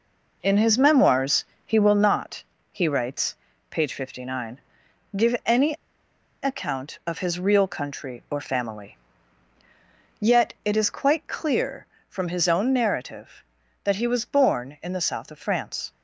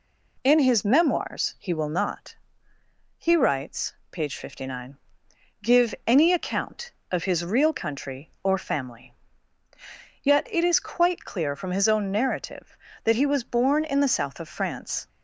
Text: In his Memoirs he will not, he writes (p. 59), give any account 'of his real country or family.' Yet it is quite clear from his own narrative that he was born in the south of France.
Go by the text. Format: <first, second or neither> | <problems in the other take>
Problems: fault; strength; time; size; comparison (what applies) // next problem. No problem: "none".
second | pauses between "Memoirs" and "he"; slight; at 1.4 s; 0.22 s long // pauses between "any" and "account"; noticeable; at 5.7 s; 0.68 s long